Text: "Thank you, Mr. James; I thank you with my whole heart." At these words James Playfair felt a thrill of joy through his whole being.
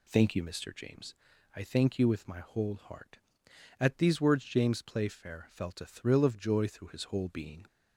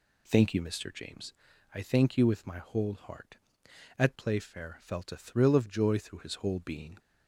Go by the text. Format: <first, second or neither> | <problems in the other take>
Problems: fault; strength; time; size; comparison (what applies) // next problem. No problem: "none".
first | skips "these words James"; at 4.1 s